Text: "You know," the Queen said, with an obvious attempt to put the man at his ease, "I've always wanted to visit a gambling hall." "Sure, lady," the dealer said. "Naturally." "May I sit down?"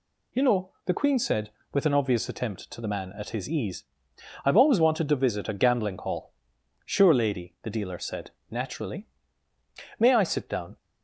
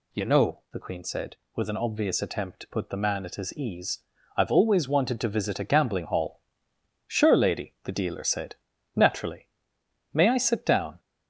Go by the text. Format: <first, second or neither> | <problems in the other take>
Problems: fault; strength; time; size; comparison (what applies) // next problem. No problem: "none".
second | skips "put"; at 2.7 s